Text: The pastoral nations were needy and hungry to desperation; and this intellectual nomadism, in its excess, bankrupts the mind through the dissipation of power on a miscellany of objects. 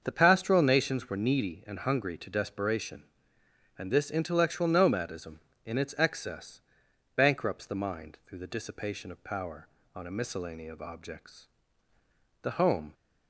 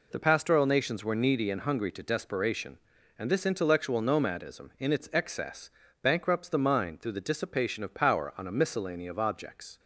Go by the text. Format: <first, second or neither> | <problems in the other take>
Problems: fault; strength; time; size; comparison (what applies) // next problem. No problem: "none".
second | starts louder than the rest; until 1.0 s; 6.5 dB // goes on to say "The home"; from 12.4 s on; 0.52 s long